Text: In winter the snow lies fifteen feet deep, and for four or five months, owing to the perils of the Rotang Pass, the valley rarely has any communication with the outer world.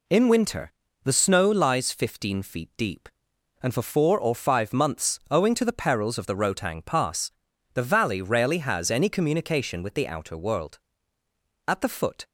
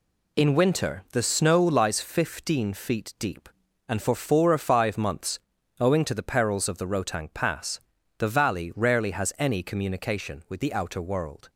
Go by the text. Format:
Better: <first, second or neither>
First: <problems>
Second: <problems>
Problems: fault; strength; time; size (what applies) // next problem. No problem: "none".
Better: second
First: pauses between "winter" and "the"; slight; at 0.7 s; 0.32 s long // goes on to say "At the foot"; from 11.6 s on; 0.60 s long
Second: none